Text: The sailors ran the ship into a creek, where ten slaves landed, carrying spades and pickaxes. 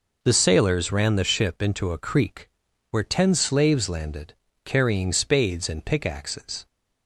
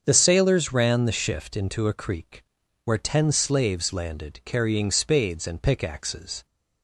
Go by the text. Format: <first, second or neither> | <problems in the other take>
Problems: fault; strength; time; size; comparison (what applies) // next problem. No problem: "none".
first | starts louder than the rest; strong; until 1.0 s; 7 dB // says "shift" for "ship"; at 1.1 s